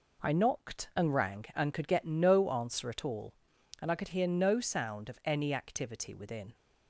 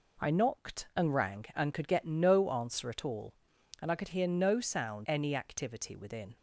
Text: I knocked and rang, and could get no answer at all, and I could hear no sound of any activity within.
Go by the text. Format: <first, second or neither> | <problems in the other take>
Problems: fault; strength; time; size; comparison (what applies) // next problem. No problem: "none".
first | skips "of"; at 5.0 s